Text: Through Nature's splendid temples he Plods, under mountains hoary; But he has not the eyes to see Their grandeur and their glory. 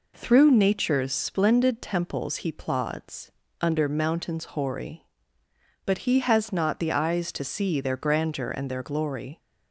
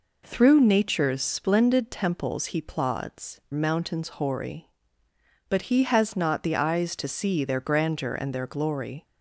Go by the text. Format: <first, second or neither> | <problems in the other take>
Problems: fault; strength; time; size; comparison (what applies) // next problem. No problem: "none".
first | skips "under"; at 3.4 s